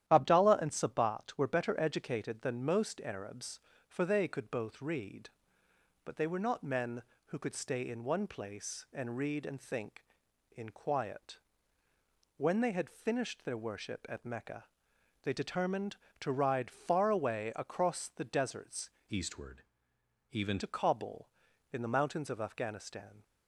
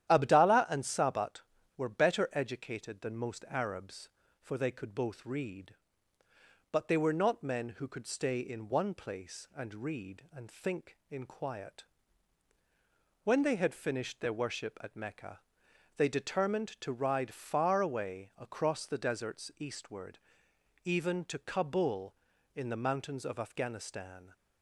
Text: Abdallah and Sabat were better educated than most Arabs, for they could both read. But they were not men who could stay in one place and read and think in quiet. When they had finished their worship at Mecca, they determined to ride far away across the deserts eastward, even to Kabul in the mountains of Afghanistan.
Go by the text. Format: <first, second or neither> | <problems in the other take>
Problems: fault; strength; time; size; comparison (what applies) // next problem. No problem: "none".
second | starts louder than the rest; strong; until 1.1 s; 11.5 dB; strong in the second // changes voice from "eastward" to "even"; from 19.0 to 20.5 s; 1.5 s long